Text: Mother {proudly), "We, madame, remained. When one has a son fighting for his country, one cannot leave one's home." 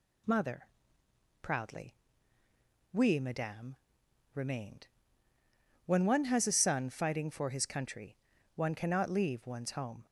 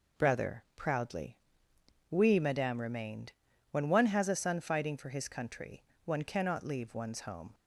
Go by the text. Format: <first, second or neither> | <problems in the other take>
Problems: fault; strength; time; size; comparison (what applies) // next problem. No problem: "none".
first | says "Brother" for "Mother"; at 0.1 s